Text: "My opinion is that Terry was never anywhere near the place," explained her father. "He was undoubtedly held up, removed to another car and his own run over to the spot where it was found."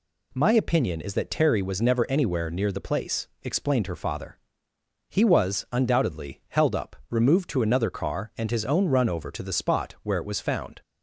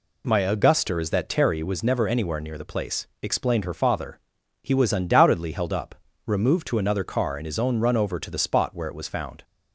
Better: first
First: none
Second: says "auguster" for "opinion"; at 0.3 s

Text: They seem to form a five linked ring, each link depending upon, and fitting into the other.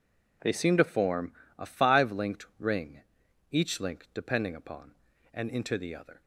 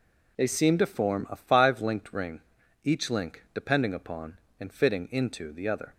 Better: second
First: pauses between "form" and "a"; slight; at 1.3 s; 0.24 s long // skips "fitting"; at 5.4 s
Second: none

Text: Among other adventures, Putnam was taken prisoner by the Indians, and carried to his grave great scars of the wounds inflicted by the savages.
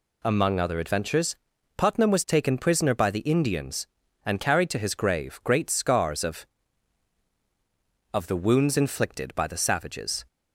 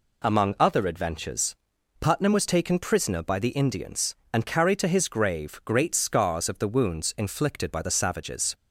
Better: second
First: says "of" twice; at 8.1 s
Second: none

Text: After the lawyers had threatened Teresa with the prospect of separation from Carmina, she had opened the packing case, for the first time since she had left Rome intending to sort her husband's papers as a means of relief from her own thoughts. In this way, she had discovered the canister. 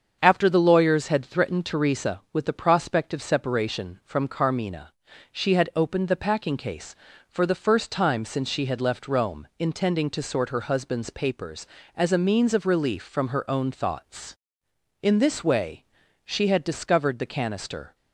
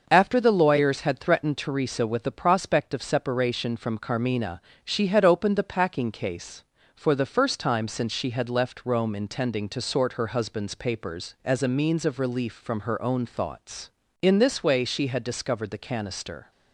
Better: neither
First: starts louder than the rest; strong; until 1.2 s; 7 dB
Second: starts louder than the rest; until 1.1 s; 6 dB

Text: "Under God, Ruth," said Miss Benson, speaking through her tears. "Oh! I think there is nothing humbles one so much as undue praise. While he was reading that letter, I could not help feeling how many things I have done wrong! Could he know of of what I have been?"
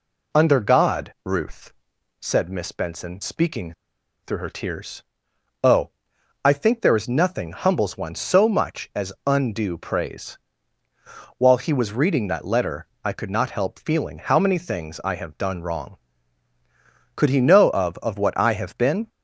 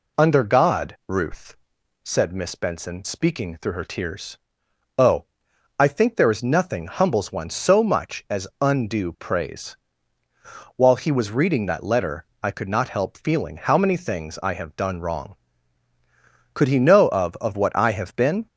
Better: second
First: pauses between "speaking" and "through"; noticeable; at 3.7 s; 0.51 s long // pauses between "as" and "undue"; slight; at 9.0 s; 0.16 s long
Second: pauses between "as" and "undue"; slight; at 8.4 s; 0.16 s long

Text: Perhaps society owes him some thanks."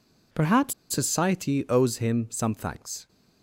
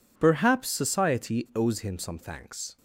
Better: second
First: pauses between "Perhaps" and "society"; slight; at 0.7 s; 0.18 s long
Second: none

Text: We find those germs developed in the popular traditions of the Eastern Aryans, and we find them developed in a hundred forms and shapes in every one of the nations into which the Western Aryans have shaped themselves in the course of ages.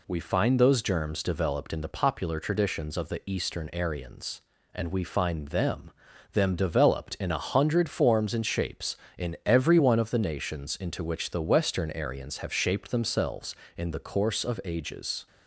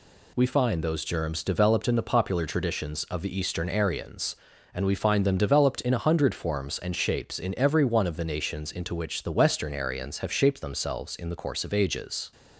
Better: second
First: says "them" twice; at 6.3 s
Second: none

